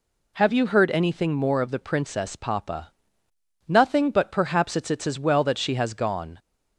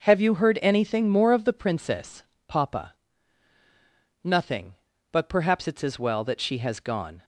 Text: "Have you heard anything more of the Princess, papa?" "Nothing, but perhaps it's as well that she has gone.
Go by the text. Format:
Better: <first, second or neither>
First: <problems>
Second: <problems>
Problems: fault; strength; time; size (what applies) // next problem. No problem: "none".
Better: second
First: says "it's" twice; at 4.8 s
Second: none